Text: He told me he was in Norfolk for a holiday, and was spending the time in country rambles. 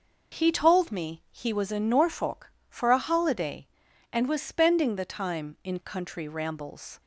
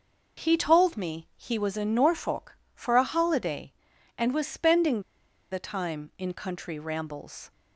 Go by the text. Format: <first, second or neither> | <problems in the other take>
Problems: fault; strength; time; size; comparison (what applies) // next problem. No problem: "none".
first | pauses between "spending" and "the"; noticeable; at 5.0 s; 0.51 s long